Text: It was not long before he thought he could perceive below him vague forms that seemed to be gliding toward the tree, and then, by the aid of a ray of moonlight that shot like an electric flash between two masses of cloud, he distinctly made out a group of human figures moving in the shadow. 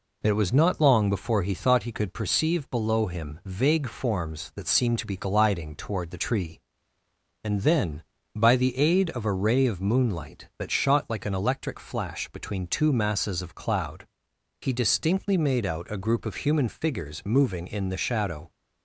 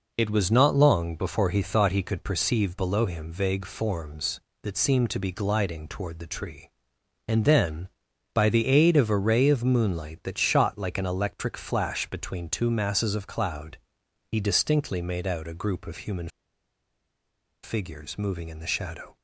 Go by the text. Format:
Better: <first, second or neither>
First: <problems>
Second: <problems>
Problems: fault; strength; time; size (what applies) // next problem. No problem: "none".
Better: first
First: none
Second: pauses between "human" and "figures"; strong; at 16.2 s; 1.3 s long